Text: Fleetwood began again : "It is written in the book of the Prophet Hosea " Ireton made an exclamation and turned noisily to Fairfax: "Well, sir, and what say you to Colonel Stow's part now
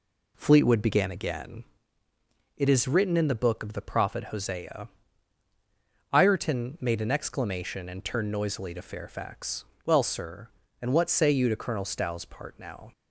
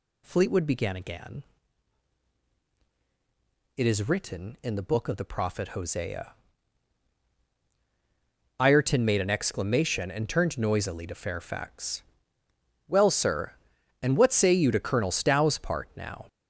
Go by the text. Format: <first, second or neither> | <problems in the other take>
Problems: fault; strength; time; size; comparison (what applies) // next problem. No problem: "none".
first | gets louder; strong; throughout; 11 dB